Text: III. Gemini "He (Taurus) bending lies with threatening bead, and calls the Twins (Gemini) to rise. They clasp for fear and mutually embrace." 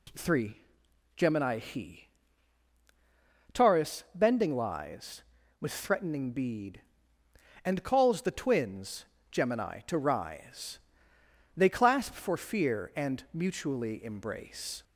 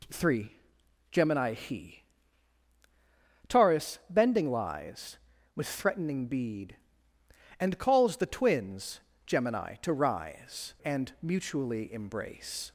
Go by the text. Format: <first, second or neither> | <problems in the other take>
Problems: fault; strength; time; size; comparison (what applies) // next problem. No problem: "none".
first | skips "They clasp for fear"; at 10.7 s